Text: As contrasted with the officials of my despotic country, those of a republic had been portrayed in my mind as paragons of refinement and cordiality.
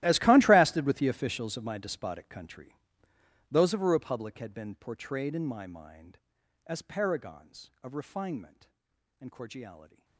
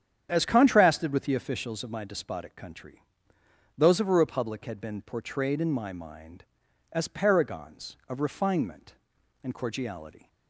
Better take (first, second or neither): second